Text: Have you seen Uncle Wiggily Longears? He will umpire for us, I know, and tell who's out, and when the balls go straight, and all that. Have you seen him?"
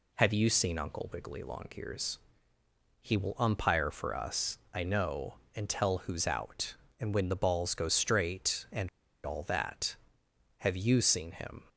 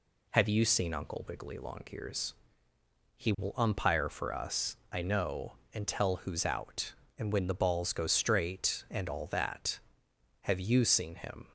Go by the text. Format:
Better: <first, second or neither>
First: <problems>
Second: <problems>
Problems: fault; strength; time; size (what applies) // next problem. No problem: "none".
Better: second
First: pauses between "and" and "all"; at 8.8 s; 0.37 s long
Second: none